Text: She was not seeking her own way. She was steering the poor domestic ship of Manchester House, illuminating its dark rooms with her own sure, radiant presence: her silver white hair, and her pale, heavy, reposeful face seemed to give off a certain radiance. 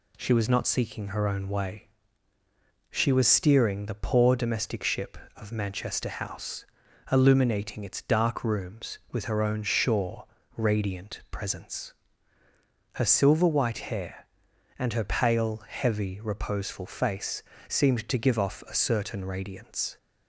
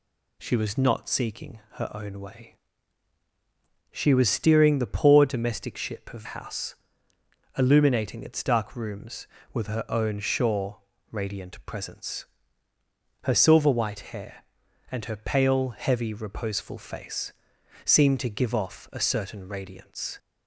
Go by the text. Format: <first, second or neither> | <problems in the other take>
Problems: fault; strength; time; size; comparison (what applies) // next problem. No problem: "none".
first | skips "Manchester"; at 6.2 s // pauses between "face" and "seemed"; noticeable; at 17.3 s; 0.54 s long; slight in the first